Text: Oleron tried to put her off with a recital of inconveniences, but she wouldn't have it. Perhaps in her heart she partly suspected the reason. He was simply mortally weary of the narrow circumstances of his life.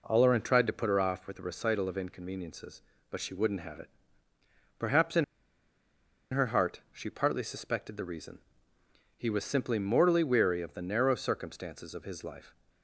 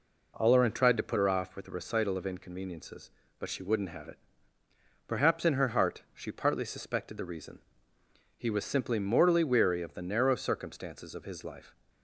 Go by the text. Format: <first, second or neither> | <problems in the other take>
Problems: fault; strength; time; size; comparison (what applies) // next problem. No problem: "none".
second | pauses between "in" and "her"; at 5.2 s; 1.0 s long